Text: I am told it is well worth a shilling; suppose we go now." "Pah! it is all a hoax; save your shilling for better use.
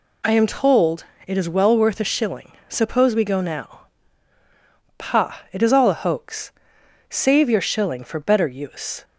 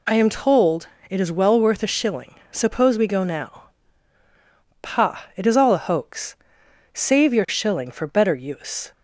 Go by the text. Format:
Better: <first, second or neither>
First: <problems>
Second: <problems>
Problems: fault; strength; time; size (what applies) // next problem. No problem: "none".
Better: neither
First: pauses between "told" and "it"; slight; at 1.0 s; 0.22 s long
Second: pauses between "told" and "it"; slight; at 0.8 s; 0.22 s long